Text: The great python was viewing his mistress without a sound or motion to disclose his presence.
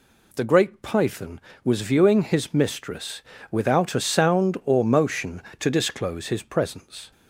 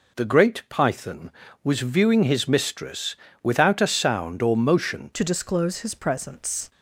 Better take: first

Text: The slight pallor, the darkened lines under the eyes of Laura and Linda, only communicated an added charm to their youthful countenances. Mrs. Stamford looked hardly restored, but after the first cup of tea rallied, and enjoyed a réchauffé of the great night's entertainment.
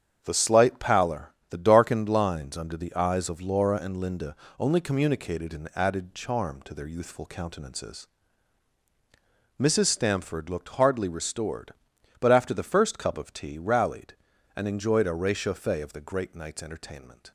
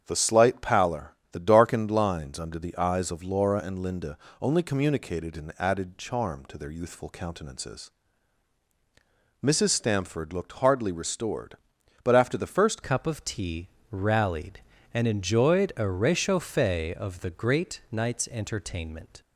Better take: first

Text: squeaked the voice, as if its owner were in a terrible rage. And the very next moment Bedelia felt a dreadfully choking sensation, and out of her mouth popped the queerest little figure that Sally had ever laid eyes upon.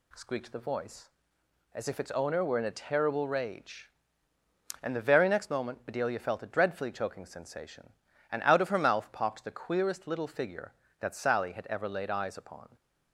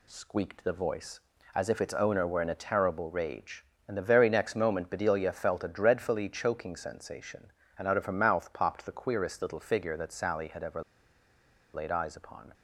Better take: first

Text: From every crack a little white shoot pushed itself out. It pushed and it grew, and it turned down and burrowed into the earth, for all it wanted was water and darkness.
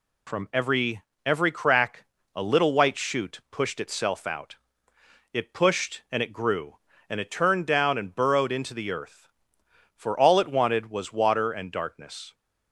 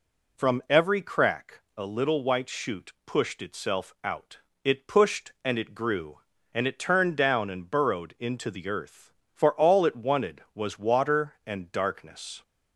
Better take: second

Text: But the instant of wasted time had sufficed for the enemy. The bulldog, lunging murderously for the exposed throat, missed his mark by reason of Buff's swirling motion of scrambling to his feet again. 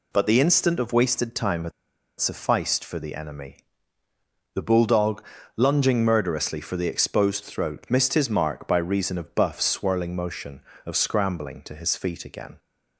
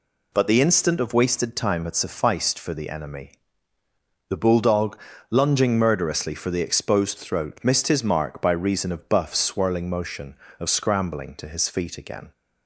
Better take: second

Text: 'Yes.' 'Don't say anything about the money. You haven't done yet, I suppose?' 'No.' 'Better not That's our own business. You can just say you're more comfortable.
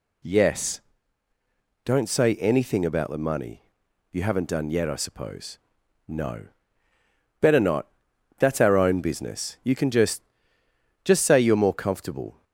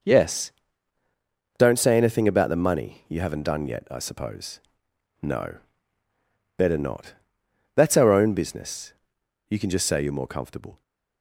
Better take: second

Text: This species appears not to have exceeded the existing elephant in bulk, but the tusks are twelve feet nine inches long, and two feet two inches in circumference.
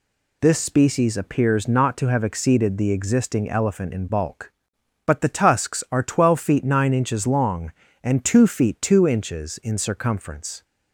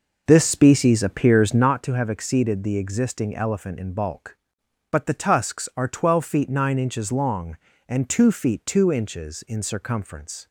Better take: first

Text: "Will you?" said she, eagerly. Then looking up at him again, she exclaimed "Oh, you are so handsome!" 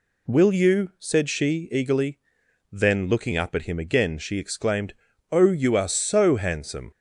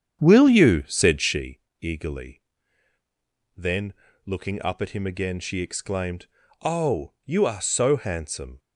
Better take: first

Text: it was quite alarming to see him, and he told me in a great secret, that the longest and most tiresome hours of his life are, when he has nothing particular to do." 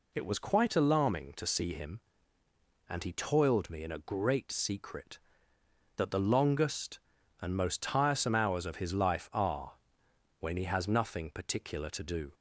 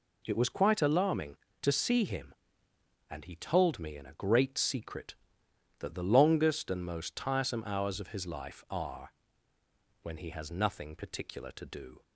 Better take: second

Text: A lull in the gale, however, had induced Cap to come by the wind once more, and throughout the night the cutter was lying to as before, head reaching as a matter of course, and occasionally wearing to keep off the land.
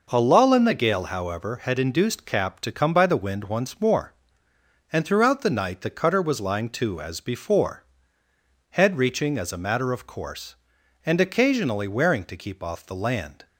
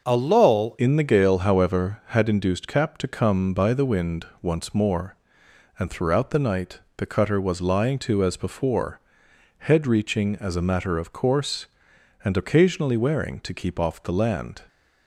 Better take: first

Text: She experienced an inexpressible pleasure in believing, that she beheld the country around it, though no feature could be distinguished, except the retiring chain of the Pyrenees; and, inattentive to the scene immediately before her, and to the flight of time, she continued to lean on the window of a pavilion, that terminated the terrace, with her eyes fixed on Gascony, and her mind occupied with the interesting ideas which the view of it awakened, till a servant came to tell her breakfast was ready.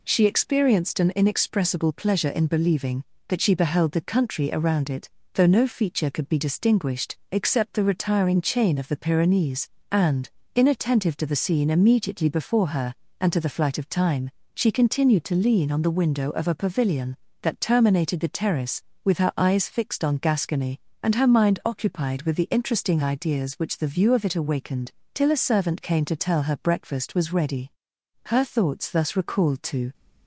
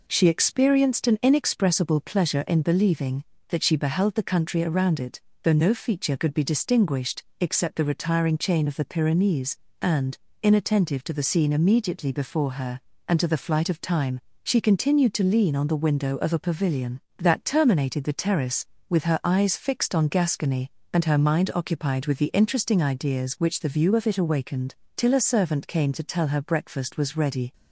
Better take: second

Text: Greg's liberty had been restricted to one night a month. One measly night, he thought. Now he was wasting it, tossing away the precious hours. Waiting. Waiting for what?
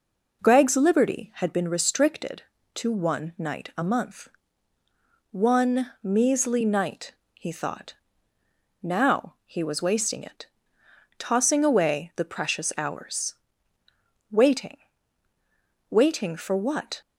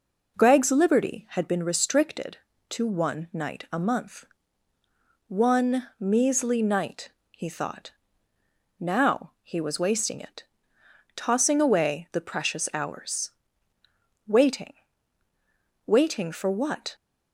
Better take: neither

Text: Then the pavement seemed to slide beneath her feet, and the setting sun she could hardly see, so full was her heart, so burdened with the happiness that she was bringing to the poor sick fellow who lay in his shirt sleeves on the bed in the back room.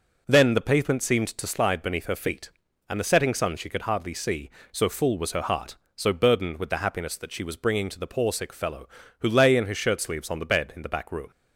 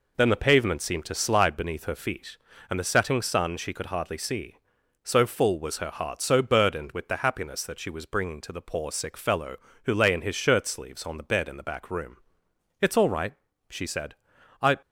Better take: first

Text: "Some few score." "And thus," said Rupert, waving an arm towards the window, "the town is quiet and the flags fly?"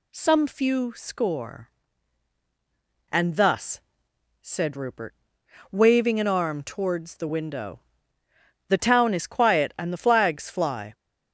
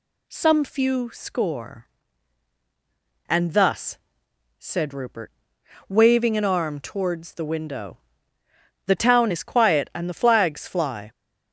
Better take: neither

